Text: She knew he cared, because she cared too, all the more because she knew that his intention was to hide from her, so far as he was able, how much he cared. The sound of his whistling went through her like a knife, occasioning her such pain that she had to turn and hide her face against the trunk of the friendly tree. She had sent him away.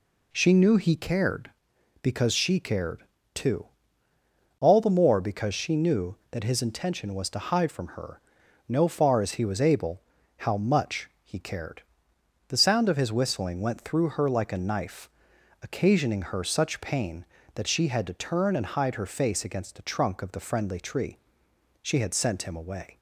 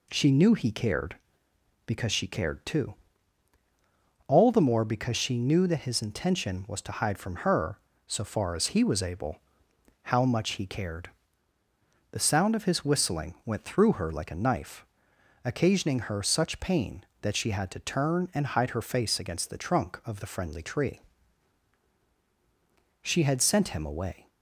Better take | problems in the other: second | pauses between "cared" and "too"; slight; at 3.0 s; 0.30 s long // says "no" for "so"; at 8.6 s

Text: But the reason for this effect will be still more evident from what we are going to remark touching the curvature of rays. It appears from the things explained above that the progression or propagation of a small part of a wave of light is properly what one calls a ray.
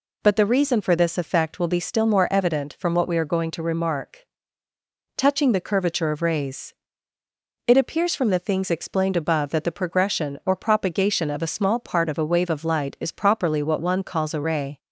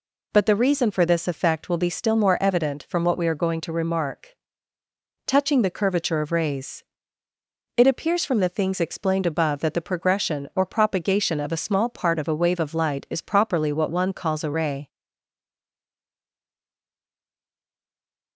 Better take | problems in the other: first | pauses between "remark" and "touching"; noticeable; at 4.3 s; 0.92 s long; noticeable in the first // stays silent after the last word; strong; from 14.8 s on; 3.5 s long

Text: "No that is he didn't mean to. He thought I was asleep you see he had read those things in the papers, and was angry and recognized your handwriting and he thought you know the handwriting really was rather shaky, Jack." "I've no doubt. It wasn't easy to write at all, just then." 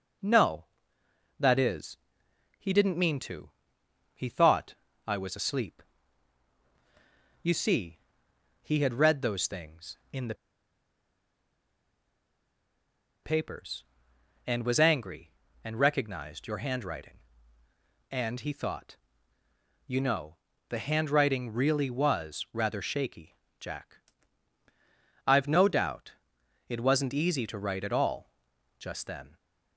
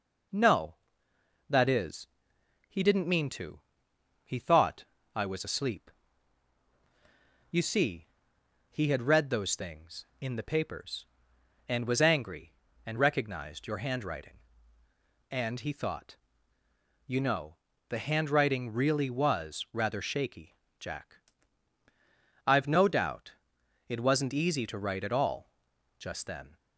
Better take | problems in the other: second | pauses between "is" and "he"; noticeable; at 1.9 s; 0.60 s long; noticeable in the second // pauses between "thought" and "I"; slight; at 4.7 s; 0.32 s long; slight in the second // pauses between "asleep" and "you"; strong; at 5.8 s; 1.6 s long; strong in the second // pauses between "see" and "he"; noticeable; at 7.9 s; 0.64 s long; noticeable in the second // pauses between "the" and "papers"; strong; at 10.3 s; 2.8 s long // pauses between "thought" and "you"; noticeable; at 18.9 s; 0.90 s long; noticeable in the second // pauses between "know" and "the"; slight; at 20.3 s; 0.32 s long; slight in the second

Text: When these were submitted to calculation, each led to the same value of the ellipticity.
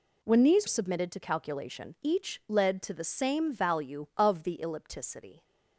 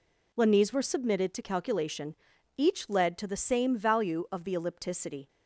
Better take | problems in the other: second | skips "were"; at 0.6 s

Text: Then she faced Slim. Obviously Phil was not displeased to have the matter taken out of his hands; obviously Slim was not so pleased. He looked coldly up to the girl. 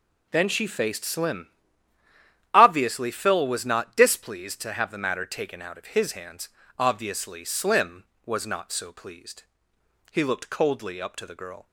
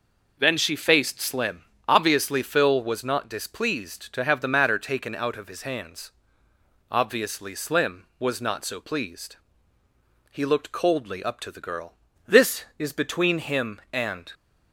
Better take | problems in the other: first | goes on to say "This is between him and"; strong; from 12.2 s on; 2.0 s long

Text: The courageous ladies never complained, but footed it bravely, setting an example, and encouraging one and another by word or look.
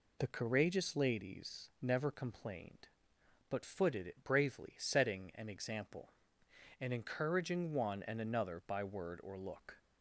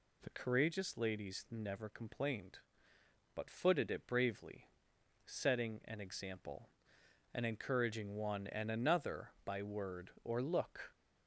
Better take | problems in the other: neither | none

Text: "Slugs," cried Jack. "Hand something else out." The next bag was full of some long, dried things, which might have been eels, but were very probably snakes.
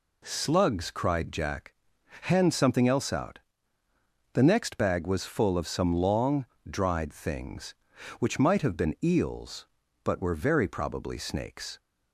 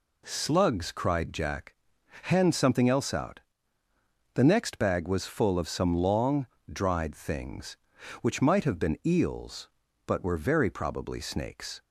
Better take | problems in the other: neither | none

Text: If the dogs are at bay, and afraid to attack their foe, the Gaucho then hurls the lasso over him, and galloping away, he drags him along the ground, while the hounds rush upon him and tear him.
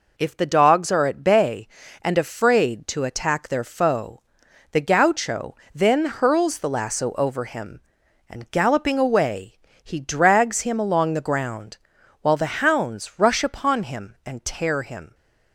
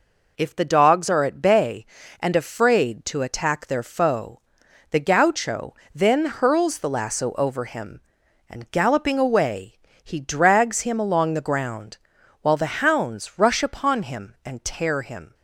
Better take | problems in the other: neither | pauses between "Gaucho" and "then"; slight; the same in both

